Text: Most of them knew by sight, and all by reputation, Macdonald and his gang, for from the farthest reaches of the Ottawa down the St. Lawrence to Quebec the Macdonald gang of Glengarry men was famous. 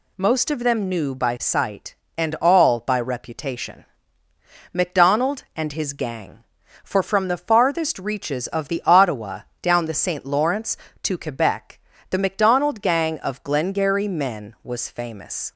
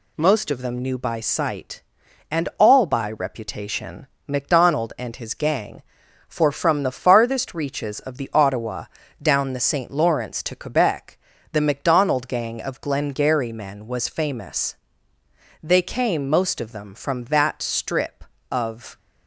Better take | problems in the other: first | pauses between "Ottawa" and "down"; slight; at 8.8 s; 0.36 s long; slight in the first // pauses between "Quebec" and "the"; slight; at 11.1 s; 0.34 s long; slight in the first // goes on to say "They came most of them from that strip of"; strong; from 15.6 s on; 3.3 s long

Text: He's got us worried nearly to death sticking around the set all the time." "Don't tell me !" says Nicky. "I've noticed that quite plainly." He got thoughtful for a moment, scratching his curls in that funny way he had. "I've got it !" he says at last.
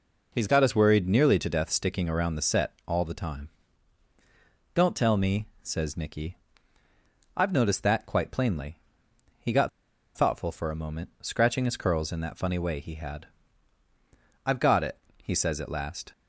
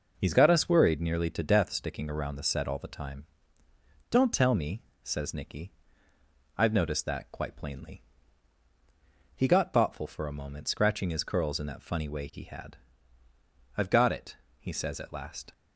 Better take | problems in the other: second | pauses between "set" and "all"; slight; at 2.7 s; 0.16 s long // pauses between "got" and "thoughtful"; noticeable; at 9.6 s; 0.46 s long

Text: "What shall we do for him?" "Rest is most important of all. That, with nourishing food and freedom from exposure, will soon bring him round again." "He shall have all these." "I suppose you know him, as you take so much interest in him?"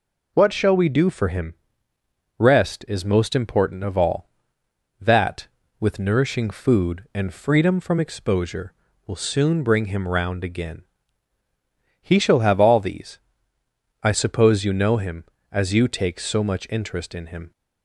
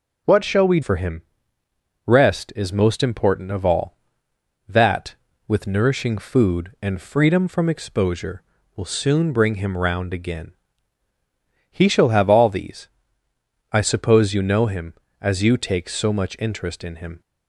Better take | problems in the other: first | skips "do"; at 0.8 s

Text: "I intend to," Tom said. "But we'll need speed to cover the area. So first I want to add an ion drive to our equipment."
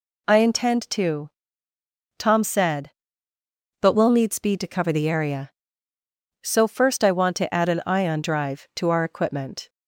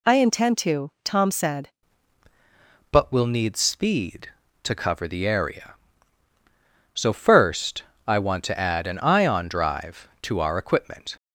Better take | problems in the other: first | changes voice at "But"; from 2.9 s on; 8.2 s long // pauses between "first" and "I"; slight; at 7.8 s; 0.24 s long

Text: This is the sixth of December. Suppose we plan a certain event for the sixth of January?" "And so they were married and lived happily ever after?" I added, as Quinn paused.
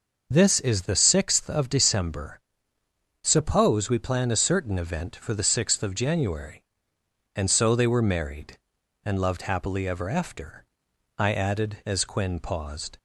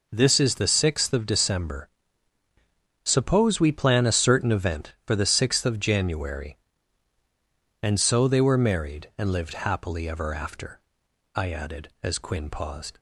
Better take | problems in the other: second | says "loved" for "lived"; at 9.2 s

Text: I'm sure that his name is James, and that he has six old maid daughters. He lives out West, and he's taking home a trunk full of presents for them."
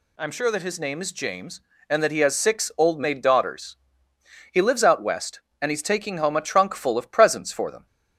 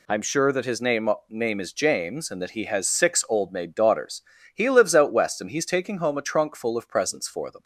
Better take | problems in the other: first | says "name" twice; at 1.2 s

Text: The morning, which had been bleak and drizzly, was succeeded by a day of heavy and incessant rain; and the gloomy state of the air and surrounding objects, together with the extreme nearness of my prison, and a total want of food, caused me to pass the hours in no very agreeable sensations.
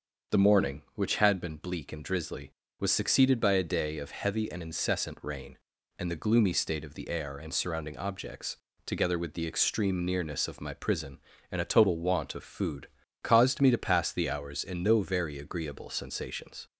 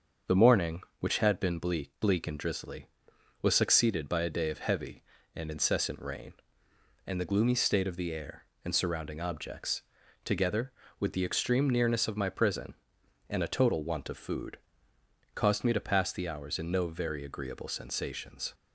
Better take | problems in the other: first | starts louder than the rest; until 1.4 s; 6.5 dB; also in the first // says "bleak" twice; at 1.9 s

